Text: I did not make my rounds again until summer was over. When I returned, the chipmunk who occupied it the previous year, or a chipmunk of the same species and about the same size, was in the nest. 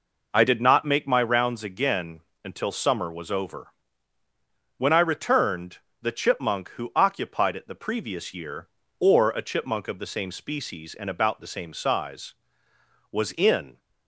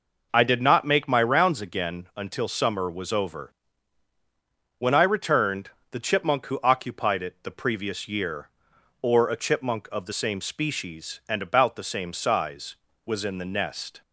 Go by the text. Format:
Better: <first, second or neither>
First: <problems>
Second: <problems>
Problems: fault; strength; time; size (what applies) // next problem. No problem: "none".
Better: second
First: pauses between "again" and "until"; slight; at 2.2 s; 0.24 s long // stops before "the nest"; at 13.7 s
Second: none